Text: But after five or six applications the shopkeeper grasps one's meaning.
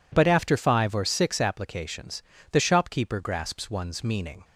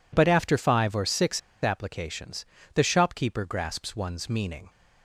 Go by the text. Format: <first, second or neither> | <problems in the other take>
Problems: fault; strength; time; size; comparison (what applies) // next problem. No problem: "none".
first | pauses between "six" and "applications"; slight; at 1.3 s; 0.23 s long // pauses between "applications" and "the"; slight; at 2.4 s; 0.30 s long; slight in the first